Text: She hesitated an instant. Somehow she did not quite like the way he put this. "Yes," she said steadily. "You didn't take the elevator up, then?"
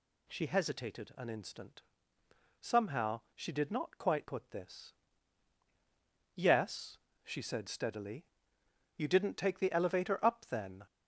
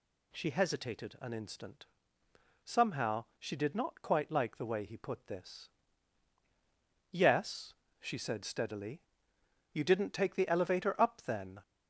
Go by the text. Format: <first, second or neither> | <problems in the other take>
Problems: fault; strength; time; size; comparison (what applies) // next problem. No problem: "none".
second | skips "like the way he"; at 4.2 s